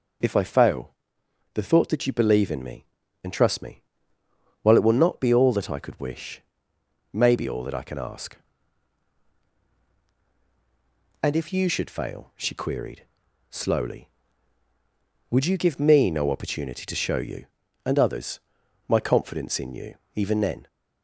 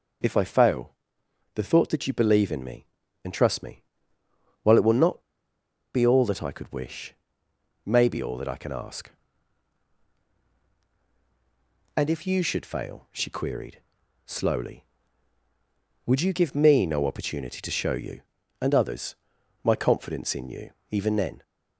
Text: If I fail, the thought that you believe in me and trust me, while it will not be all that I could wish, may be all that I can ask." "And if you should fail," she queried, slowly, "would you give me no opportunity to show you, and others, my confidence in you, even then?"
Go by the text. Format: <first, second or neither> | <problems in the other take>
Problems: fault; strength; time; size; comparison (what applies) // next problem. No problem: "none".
first | pauses between "not" and "be"; noticeable; at 5.2 s; 0.74 s long